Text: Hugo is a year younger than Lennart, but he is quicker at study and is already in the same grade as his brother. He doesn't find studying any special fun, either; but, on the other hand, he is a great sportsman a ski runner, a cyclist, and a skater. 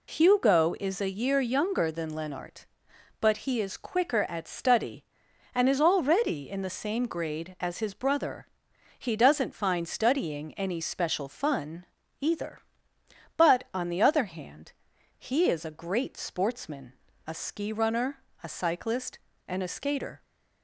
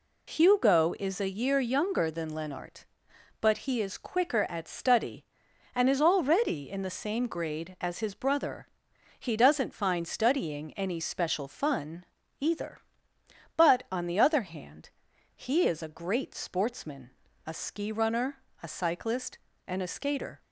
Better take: neither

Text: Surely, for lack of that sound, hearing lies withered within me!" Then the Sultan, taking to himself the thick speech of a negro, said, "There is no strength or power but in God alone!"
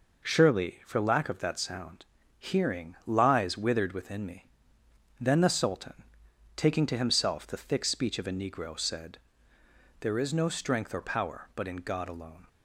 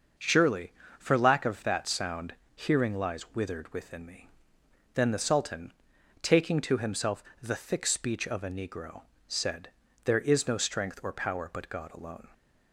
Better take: first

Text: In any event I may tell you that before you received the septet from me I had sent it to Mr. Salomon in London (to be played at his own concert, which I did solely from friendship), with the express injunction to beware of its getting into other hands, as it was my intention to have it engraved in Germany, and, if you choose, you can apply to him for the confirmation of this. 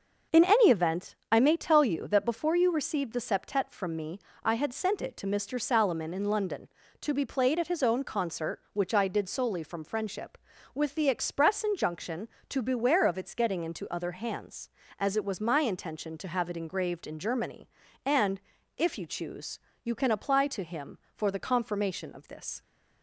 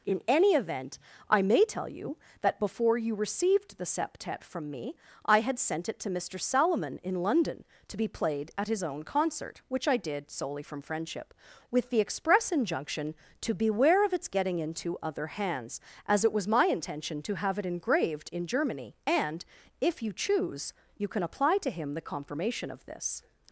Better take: first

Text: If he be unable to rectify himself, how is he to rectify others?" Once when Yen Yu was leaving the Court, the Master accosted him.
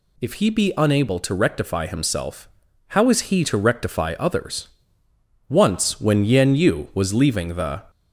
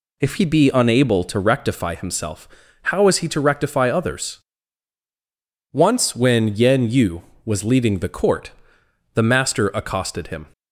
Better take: second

